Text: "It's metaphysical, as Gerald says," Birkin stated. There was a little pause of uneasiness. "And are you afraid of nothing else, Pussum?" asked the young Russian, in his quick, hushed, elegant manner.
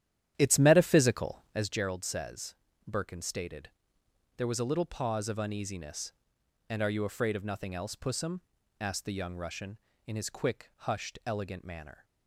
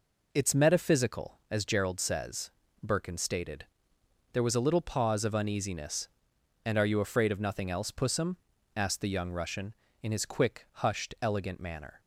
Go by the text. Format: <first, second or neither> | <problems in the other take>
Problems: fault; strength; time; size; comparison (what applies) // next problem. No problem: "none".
second | starts louder than the rest; strong; until 1.7 s; 11 dB